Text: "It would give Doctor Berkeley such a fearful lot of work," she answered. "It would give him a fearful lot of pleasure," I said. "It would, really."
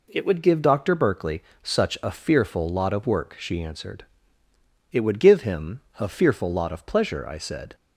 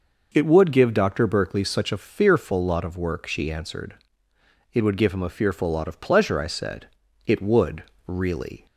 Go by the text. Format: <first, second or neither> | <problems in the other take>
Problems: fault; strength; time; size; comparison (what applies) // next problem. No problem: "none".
second | pauses between "Berkeley" and "such"; slight; at 1.4 s; 0.18 s long // pauses between "him" and "a"; slight; at 5.8 s; 0.18 s long // stops before "It would really"; at 7.7 s